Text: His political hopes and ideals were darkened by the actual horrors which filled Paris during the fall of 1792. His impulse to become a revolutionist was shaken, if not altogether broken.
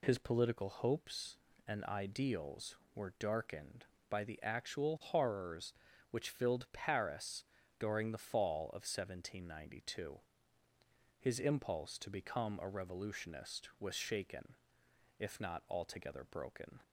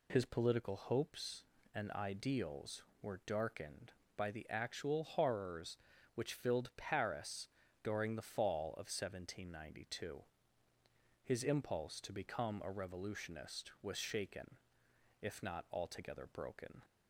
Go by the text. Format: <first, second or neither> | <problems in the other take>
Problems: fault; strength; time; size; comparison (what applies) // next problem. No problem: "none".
neither | pauses between "Paris" and "during"; slight; the same in both